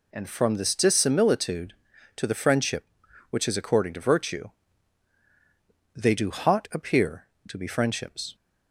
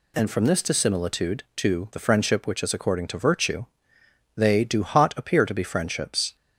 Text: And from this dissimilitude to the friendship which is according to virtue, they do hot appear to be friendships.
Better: neither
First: none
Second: none

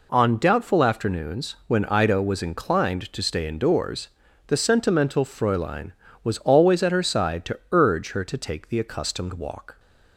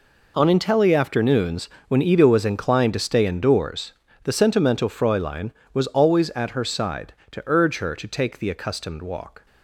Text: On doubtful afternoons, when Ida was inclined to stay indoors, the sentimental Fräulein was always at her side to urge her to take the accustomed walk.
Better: first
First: none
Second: says "intelli" for "doubtful"; at 0.4 s

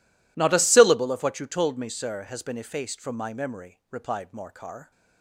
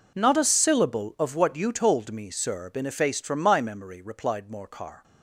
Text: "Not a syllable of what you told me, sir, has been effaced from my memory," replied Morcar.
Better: first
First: none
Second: skips "has"; at 2.6 s

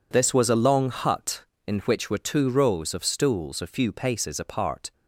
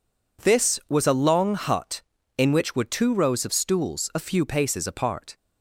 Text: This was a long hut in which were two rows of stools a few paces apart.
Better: neither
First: none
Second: none

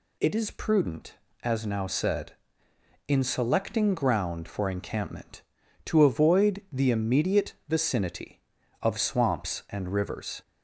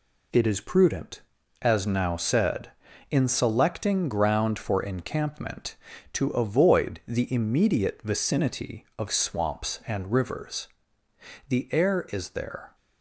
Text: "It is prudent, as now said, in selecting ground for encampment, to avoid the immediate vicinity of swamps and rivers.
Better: first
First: none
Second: goes on to say "The air is there"; noticeable; from 11.4 s on; 1.2 s long

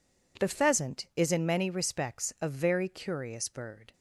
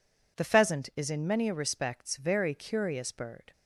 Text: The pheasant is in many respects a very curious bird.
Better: first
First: none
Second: skips "a"; at 2.1 s

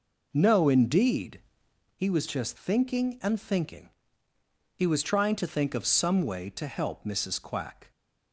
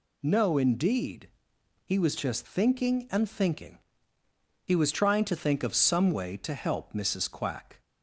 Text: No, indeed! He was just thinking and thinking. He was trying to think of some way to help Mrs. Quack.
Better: second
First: starts louder than the rest; noticeable; until 1.8 s; 4.5 dB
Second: none

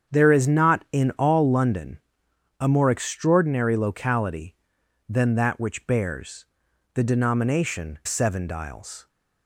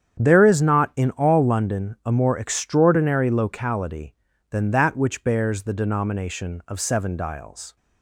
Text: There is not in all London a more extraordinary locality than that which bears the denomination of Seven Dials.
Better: second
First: starts louder than the rest; strong; until 1.2 s; 7.5 dB // pauses between "London" and "a"; noticeable; at 1.9 s; 0.62 s long // pauses between "bears" and "the"; noticeable; at 6.4 s; 0.48 s long // skips "of"; at 8.0 s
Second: starts louder than the rest; strong; until 1.2 s; 8.5 dB

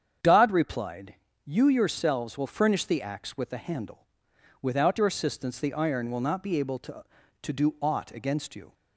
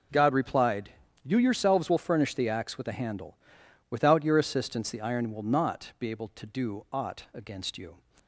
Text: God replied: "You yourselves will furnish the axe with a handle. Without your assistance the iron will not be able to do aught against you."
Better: second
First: starts louder than the rest; strong; until 1.5 s; 8 dB // says "to" twice; at 7.4 s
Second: none

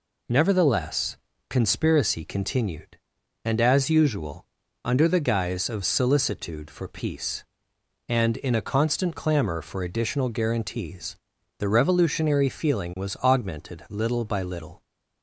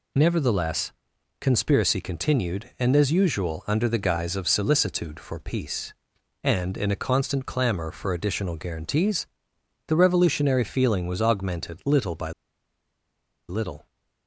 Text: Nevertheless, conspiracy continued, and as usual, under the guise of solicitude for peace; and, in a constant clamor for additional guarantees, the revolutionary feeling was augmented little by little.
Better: first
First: none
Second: pauses between "by" and "little"; at 12.3 s; 1.1 s long

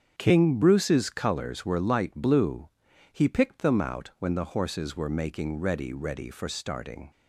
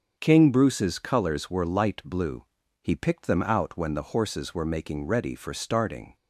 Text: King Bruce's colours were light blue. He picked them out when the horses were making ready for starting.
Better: second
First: starts louder than the rest; strong; until 1.1 s; 7.5 dB // says "ready" twice; at 5.9 s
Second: starts louder than the rest; strong; until 1.2 s; 7 dB

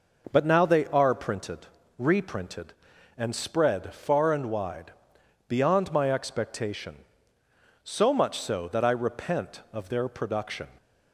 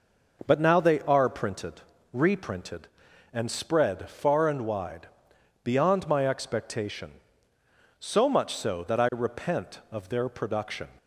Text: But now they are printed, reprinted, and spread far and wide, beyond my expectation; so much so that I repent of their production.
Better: neither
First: none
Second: none

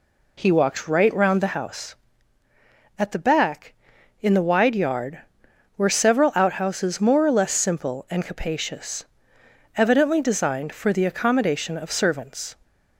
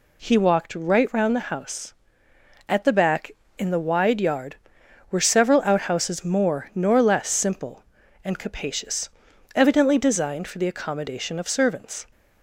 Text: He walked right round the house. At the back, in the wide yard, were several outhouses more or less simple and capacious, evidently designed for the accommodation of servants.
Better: first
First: none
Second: says "nor" for "or"; at 6.7 s

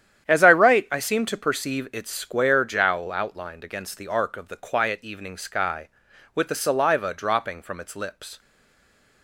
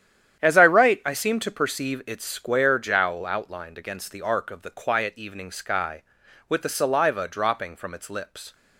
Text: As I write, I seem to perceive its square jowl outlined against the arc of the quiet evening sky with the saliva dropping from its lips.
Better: second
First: starts louder than the rest; strong; until 1.2 s; 9.5 dB // stays silent after the last word; slight; from 8.3 s on; 0.9 s long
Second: starts louder than the rest; strong; until 1.4 s; 9.5 dB

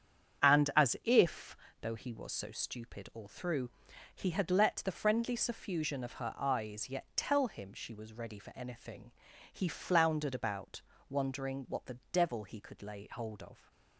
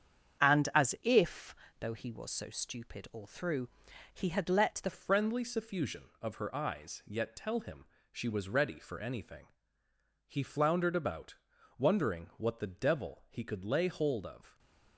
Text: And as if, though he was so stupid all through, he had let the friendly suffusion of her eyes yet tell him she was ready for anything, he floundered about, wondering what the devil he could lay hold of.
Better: first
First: starts louder than the rest; strong; until 1.5 s; 8.5 dB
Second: starts louder than the rest; strong; until 1.5 s; 8 dB // changes voice at "friendly"; from 4.9 s on; 9.6 s long // pauses between "him" and "she"; slight; at 7.8 s; 0.26 s long

